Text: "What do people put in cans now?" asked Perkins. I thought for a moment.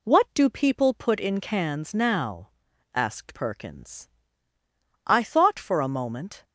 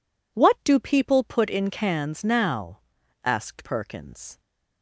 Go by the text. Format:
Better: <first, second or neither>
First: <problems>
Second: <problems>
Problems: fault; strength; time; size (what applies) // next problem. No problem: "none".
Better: first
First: none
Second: stops before "I thought for a moment"; at 4.3 s